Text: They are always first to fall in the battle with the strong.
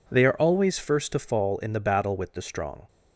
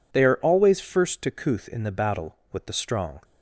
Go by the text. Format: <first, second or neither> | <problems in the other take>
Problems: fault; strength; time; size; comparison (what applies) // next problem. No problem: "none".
first | says "couth" for "fall"; at 1.3 s